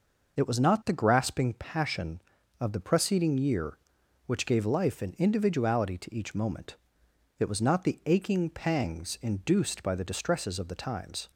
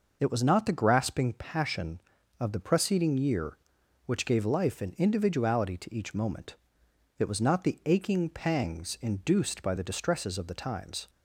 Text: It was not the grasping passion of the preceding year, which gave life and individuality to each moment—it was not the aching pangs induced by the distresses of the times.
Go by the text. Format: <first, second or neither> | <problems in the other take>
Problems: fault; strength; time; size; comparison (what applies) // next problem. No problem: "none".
neither | none